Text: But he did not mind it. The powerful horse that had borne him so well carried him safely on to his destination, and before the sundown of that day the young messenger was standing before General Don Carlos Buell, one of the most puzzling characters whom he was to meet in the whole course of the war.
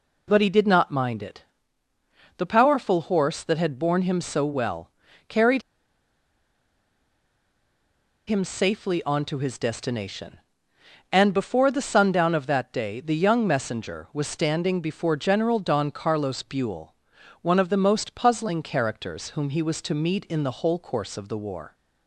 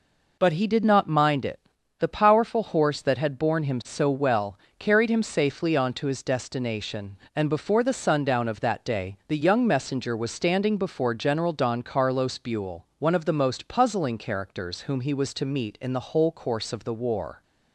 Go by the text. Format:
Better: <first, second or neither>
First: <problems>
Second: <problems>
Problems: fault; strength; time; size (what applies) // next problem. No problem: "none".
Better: second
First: pauses between "well" and "carried"; slight; at 4.9 s; 0.36 s long // pauses between "carried" and "him"; strong; at 5.6 s; 2.6 s long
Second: pauses between "well" and "carried"; slight; at 4.5 s; 0.20 s long